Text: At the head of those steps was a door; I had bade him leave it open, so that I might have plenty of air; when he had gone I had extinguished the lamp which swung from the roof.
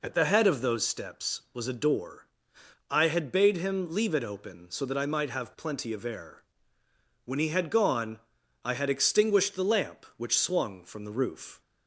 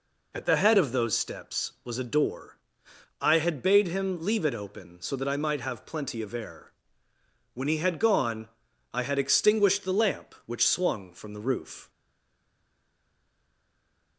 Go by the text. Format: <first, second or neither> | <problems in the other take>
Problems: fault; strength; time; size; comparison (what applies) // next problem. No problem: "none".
first | pauses between "gone" and "I"; noticeable; at 8.4 s; 0.46 s long; noticeable in the first // stays silent after the last word; from 11.8 s on; 2.3 s long